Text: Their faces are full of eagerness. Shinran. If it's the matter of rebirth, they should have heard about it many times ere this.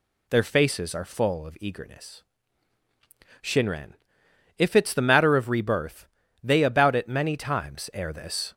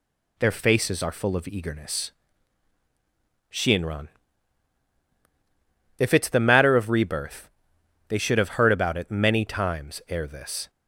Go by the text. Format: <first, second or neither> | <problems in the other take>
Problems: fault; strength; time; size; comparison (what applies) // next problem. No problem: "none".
second | skips "should have heard"; at 6.6 s